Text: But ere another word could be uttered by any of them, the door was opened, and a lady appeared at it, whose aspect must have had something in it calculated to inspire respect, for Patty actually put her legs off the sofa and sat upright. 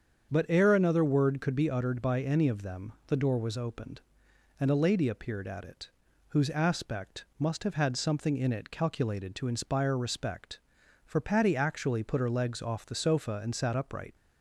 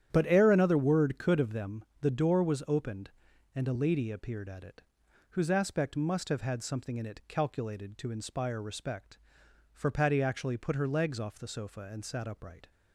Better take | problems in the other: first | starts louder than the rest; strong; until 1.1 s; 10 dB; strong in the first // skips "be uttered by any"; at 1.3 s

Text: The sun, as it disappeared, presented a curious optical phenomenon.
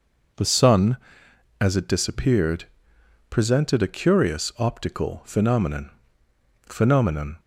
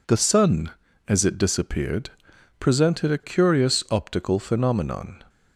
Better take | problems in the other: second | says "phenomenon" twice; at 6.6 s

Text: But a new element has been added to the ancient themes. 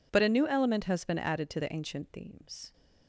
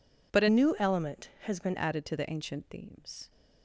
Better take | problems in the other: first | changes voice from "new" to "been"; from 0.4 to 1.7 s; 1.3 s long

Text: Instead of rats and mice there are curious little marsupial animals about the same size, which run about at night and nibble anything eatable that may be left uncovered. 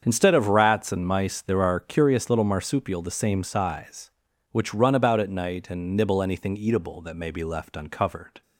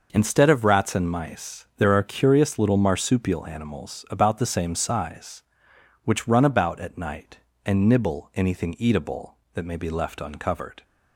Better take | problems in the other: second | starts louder than the rest; strong; until 1.0 s; 7.5 dB // skips "animals about"; at 3.0 s

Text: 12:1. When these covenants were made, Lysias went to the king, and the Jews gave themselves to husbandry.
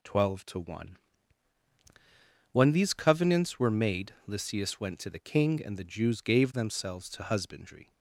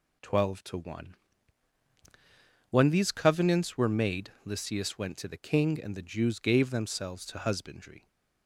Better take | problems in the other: neither | none

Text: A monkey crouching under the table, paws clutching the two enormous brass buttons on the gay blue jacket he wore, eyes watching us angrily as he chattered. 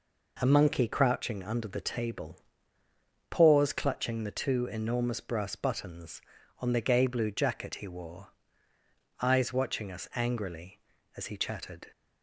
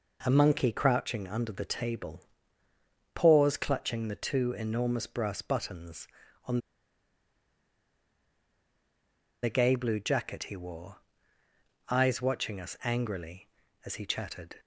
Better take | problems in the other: first | pauses between "on" and "the"; strong; at 6.5 s; 2.8 s long

